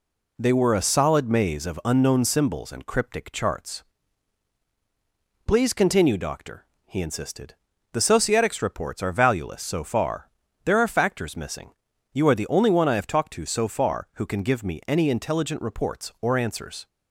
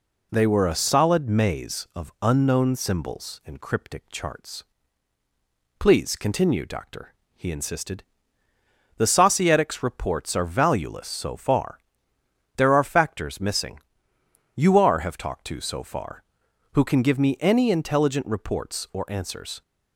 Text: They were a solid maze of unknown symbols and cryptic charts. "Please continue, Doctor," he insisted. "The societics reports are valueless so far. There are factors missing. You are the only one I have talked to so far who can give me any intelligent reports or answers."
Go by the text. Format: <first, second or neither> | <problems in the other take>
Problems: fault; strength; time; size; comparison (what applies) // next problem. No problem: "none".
first | skips "the only one I"; at 14.9 s